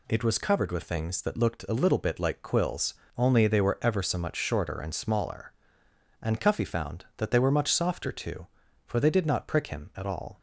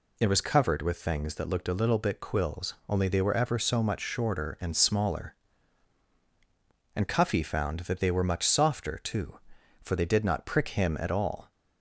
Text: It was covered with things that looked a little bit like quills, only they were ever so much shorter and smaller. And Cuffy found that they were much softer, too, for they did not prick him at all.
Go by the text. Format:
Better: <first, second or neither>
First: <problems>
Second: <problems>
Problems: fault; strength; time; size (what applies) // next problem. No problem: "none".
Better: first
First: none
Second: skips "like"; at 2.2 s